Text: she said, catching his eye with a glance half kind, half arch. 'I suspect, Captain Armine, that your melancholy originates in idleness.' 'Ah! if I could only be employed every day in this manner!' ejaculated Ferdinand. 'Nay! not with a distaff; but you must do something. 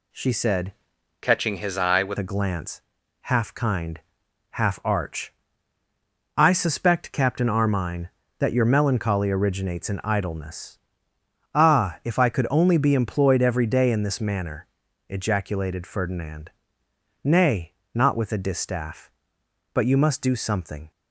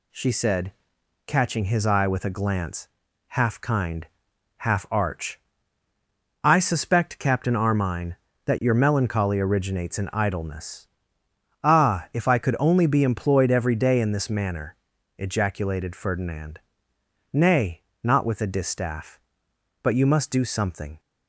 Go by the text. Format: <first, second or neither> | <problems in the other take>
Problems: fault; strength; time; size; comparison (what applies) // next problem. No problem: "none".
second | changes voice from "catching" to "with"; from 1.2 to 2.1 s; 0.9 s long // pauses between "glance" and "half"; noticeable; at 2.8 s; 0.48 s long; noticeable in the second